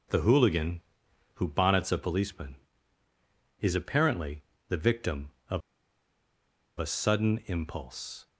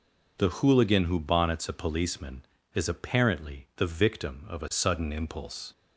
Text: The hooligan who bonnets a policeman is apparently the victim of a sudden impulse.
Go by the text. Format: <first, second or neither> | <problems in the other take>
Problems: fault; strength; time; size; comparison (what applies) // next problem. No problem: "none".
second | pauses between "apparently" and "the"; slight; at 4.4 s; 0.28 s long // pauses between "of" and "a"; at 5.6 s; 1.1 s long